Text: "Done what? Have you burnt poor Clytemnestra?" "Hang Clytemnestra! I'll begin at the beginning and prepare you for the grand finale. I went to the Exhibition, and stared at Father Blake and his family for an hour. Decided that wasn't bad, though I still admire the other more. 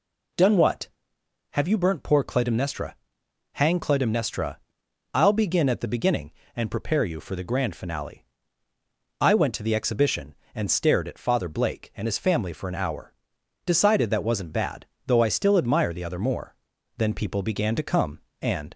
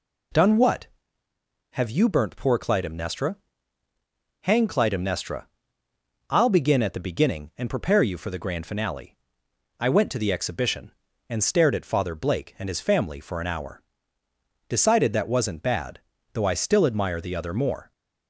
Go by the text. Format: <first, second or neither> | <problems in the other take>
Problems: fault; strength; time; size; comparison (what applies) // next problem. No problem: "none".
second | goes on to say "Then people began to come and"; strong; from 16.9 s on; 1.7 s long